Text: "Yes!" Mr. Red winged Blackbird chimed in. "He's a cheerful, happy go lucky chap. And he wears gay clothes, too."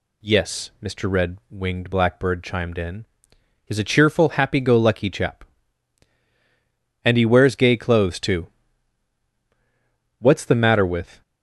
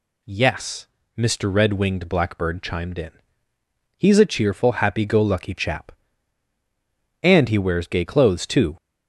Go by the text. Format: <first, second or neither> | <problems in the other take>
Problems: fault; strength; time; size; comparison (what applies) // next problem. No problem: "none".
second | goes on to say "What's the matter with"; noticeable; from 10.1 s on; 1.0 s long